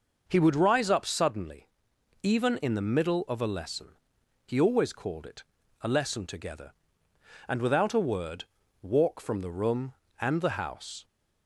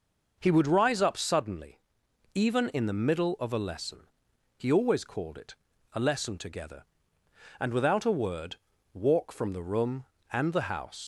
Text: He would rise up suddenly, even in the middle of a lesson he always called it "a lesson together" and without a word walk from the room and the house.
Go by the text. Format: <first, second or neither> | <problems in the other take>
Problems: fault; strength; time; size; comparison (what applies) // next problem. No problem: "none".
first | pauses between "lesson" and "he"; noticeable; at 4.0 s; 0.50 s long; noticeable in the first // pauses between "it" and "a"; at 5.5 s; 0.38 s long; also in the first // pauses between "word" and "walk"; at 8.5 s; 0.40 s long; also in the first // leaves "house" unfinished; at 11.0 s; 90 ms